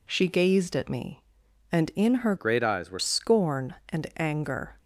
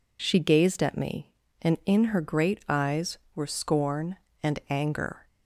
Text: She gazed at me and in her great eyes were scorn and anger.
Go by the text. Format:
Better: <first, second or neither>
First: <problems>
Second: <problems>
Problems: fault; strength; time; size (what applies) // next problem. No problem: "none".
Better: second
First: changes voice from "great" to "were"; from 2.3 to 2.9 s; 0.6 s long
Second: none